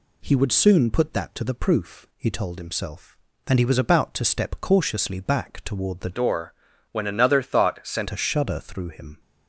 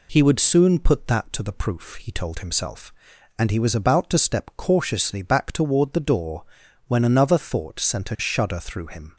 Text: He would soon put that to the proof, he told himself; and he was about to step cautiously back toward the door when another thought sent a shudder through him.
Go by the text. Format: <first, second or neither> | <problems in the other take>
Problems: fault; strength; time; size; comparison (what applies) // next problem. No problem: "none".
second | changes voice from "door" to "sent"; from 6.1 to 8.0 s; 1.9 s long // pauses between "door" and "when"; at 6.5 s; 0.38 s long; noticeable in the second